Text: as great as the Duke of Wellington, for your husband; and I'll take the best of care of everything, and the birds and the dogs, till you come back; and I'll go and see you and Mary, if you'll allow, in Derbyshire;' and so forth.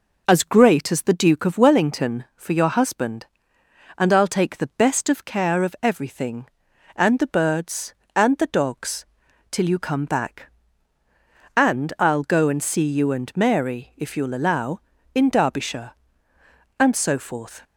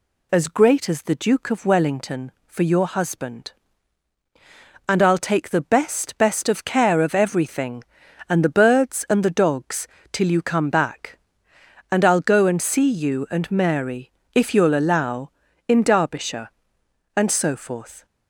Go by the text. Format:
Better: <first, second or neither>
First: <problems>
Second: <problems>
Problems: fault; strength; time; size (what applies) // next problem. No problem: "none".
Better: first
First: none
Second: says "best" twice; at 6.1 s